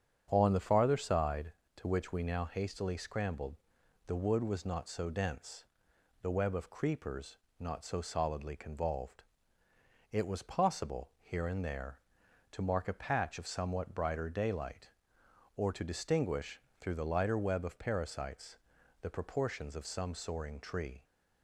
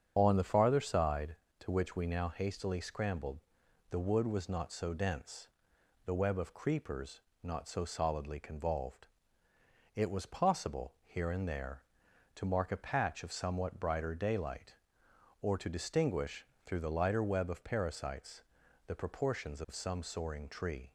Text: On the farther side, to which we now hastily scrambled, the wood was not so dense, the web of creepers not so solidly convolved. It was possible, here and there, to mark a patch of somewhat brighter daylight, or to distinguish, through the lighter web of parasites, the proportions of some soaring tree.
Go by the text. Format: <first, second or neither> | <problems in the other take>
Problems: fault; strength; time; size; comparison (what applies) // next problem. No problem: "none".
first | loses the start of "On"; at 0.1 s; 50 ms // starts louder than the rest; strong; until 1.1 s; 7.5 dB; strong in the first // pauses between "creepers" and "not"; slight; at 7.2 s; 0.22 s long; slight in the first